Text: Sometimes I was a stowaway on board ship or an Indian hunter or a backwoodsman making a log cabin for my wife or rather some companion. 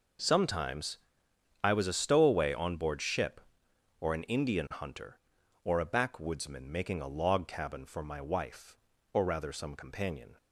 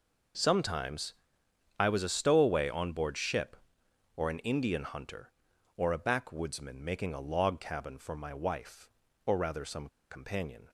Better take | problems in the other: first | pauses between "Sometimes" and "I"; noticeable; at 1.1 s; 0.66 s long; noticeable in the first // pauses between "some" and "companion"; slight; at 9.8 s; 0.22 s long

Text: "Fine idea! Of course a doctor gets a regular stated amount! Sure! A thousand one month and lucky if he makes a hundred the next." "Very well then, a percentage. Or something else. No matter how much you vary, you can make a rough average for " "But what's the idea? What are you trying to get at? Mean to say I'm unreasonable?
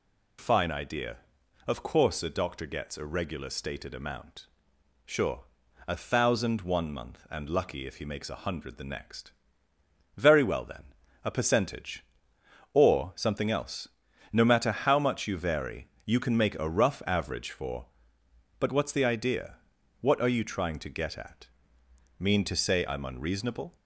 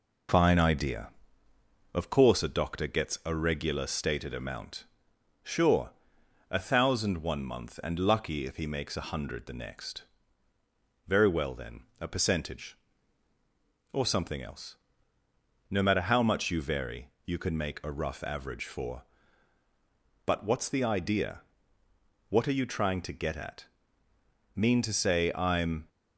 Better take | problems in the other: first | stops before "unreasonable"; at 25.8 s

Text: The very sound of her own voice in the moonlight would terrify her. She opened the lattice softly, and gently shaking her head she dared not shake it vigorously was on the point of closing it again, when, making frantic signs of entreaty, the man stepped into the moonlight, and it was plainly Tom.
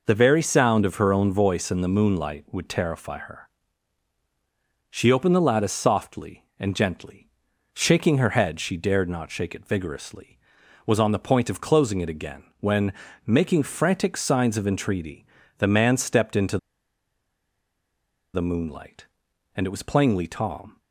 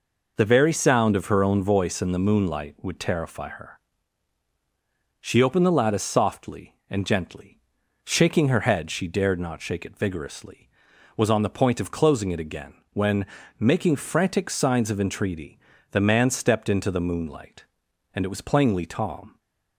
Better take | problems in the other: second | pauses between "gently" and "shaking"; noticeable; at 7.2 s; 0.46 s long; noticeable in the second // pauses between "into" and "the"; strong; at 16.5 s; 1.7 s long

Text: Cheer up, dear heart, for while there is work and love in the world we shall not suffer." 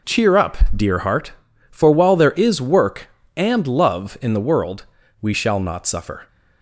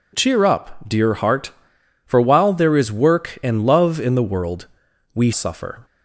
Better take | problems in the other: first | pauses between "world" and "we"; noticeable; at 4.6 s; 0.46 s long; also in the first // skips "shall not"; at 5.3 s

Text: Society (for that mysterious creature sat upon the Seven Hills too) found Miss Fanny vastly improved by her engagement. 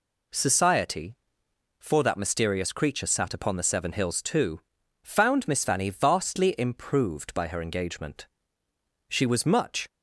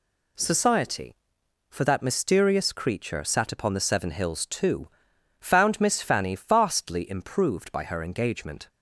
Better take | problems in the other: second | goes on to say "She was much"; noticeable; from 9.0 s on; 0.80 s long

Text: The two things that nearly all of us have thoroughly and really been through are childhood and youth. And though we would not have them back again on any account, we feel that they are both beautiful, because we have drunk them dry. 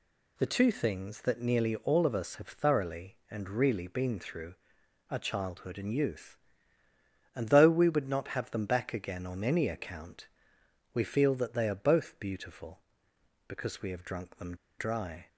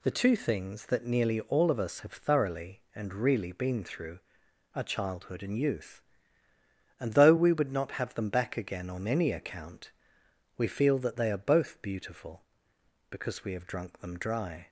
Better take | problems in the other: second | pauses between "them" and "dry"; slight; at 14.5 s; 0.24 s long

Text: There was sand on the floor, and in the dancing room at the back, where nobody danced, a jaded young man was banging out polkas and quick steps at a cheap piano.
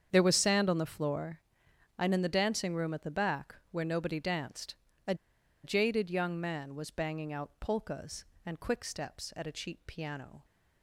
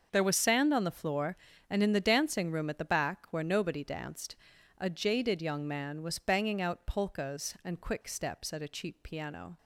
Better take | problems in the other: second | starts louder than the rest; strong; until 1.1 s; 8 dB; also in the second // pauses between "a" and "jaded"; noticeable; at 5.1 s; 0.49 s long

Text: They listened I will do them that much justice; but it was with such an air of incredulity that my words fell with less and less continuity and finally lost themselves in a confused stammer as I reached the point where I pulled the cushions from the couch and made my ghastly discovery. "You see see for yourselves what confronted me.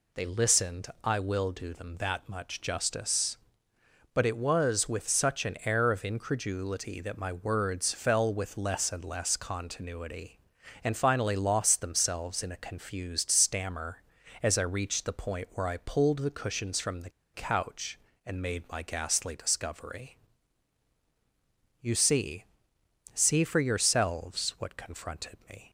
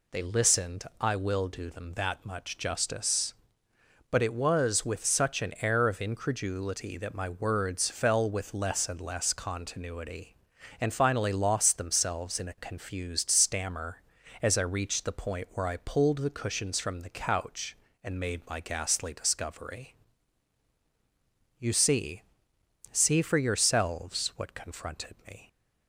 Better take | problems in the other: second | pauses between "listened" and "I"; slight; at 0.8 s; 0.16 s long; slight in the second // pauses between "the" and "couch"; slight; at 17.1 s; 0.23 s long // pauses between "see" and "see"; noticeable; at 22.4 s; 0.68 s long; noticeable in the second

